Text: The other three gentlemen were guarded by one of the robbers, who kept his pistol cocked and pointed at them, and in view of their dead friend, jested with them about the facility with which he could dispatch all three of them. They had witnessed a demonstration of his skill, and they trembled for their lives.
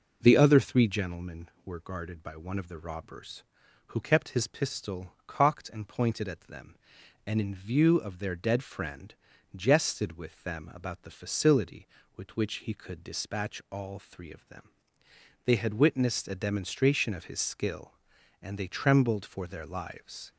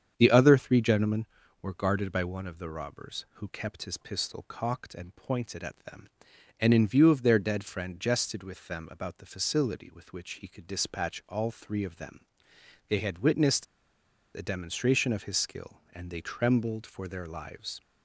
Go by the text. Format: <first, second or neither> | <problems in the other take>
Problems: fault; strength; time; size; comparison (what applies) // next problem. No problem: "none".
first | starts louder than the rest; strong; until 1.1 s; 8 dB // pauses between "witnessed" and "a"; noticeable; at 13.6 s; 0.70 s long